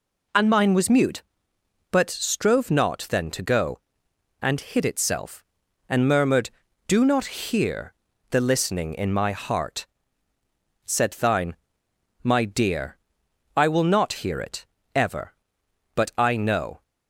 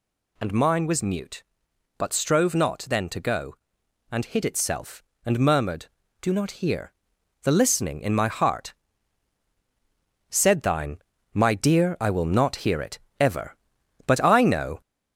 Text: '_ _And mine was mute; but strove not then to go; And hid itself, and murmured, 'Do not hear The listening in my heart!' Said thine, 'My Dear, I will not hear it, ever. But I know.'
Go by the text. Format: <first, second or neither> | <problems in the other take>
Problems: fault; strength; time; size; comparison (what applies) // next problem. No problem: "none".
first | gets louder; slight; throughout; 3 dB // pauses between "hear" and "The"; noticeable; at 6.9 s; 0.48 s long; slight in the first